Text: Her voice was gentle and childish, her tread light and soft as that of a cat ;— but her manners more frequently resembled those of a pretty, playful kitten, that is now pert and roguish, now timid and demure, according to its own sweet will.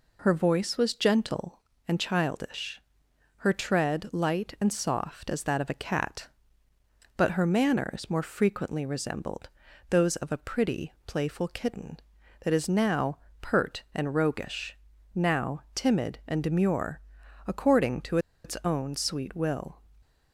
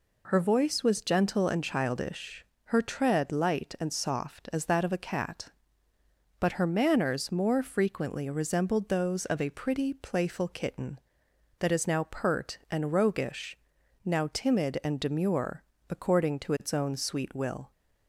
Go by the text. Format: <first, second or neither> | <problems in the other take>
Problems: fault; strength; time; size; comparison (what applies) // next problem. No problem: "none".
second | pauses between "resembled" and "those"; at 9.4 s; 0.40 s long // pauses between "now" and "pert"; slight; at 13.1 s; 0.24 s long // pauses between "to" and "its"; slight; at 18.1 s; 0.26 s long